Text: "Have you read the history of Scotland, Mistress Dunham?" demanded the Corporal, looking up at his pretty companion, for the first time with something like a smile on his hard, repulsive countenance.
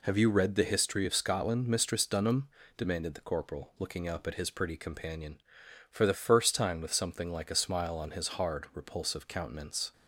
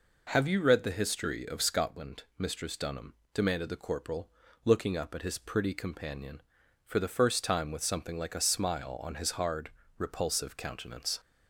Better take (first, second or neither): neither